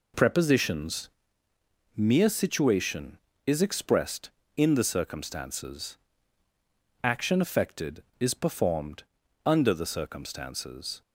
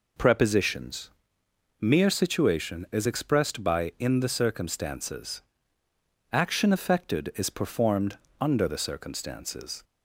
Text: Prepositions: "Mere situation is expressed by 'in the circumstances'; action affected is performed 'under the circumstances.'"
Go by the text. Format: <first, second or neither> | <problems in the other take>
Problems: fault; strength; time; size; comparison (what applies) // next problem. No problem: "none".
second | skips "by"; at 4.4 s // pauses between "performed" and "under"; at 9.0 s; 0.42 s long; slight in the second